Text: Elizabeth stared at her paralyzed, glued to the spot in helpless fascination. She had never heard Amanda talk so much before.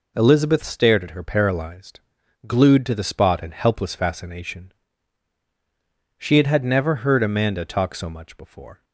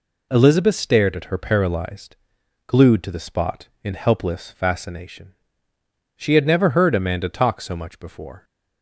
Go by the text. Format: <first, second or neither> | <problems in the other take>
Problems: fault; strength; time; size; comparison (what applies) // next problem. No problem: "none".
second | says "had" twice; at 6.4 s